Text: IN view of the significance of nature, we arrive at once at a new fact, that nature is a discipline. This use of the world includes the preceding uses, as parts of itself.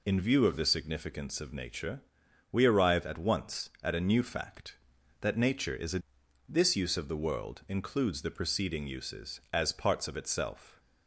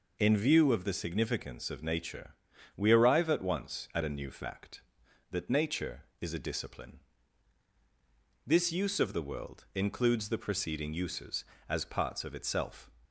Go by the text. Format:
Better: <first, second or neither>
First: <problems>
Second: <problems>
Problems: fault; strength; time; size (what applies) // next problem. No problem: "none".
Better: second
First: skips "discipline"; at 6.2 s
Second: none